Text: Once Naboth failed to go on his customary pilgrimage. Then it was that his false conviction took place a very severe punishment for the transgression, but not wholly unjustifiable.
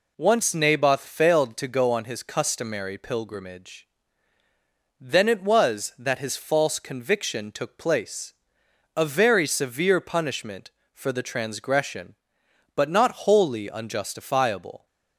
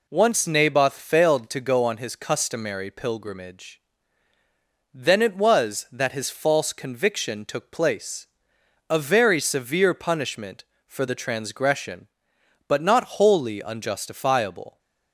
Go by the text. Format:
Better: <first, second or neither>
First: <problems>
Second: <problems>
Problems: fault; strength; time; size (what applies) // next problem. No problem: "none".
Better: neither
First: pauses between "place" and "a"; noticeable; at 8.3 s; 0.62 s long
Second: pauses between "place" and "a"; noticeable; at 8.2 s; 0.62 s long